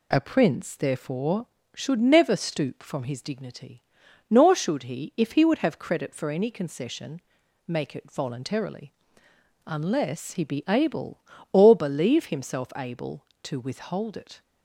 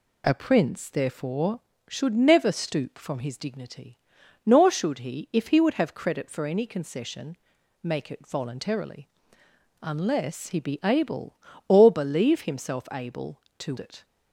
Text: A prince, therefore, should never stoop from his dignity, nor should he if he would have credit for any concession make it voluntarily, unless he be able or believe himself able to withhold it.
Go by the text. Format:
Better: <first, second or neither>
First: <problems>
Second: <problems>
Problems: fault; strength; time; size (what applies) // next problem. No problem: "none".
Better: first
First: pauses between "concession" and "make"; noticeable; at 7.2 s; 0.46 s long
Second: pauses between "concession" and "make"; noticeable; at 7.3 s; 0.46 s long // skips "withhold"; at 13.7 s